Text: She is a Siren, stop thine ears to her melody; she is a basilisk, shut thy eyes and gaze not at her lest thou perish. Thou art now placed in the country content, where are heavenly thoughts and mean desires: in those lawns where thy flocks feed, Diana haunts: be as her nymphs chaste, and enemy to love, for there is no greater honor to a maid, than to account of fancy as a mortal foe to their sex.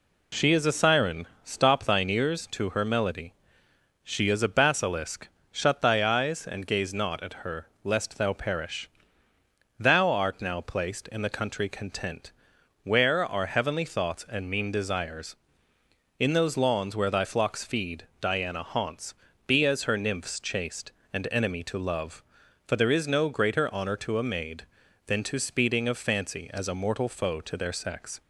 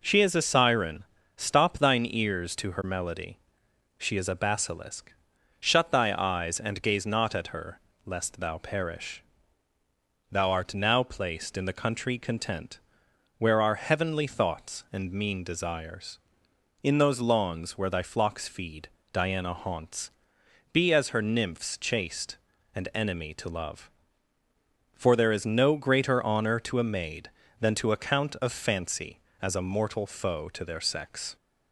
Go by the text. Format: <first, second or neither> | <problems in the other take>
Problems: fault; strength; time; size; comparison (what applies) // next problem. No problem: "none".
second | pauses between "her" and "lest"; slight; at 7.6 s; 0.16 s long; slight in the second // says "speeding" for "account"; at 25.3 s